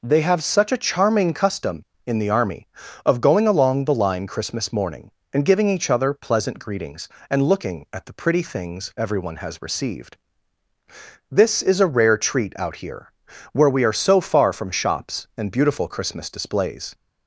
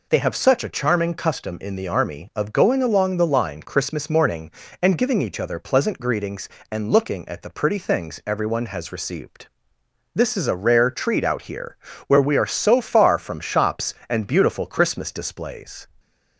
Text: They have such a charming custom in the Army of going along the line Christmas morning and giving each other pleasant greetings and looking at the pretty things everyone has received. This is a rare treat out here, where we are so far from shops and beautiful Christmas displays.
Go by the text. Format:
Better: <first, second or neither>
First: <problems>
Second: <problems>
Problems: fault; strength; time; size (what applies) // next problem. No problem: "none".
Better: neither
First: none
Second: none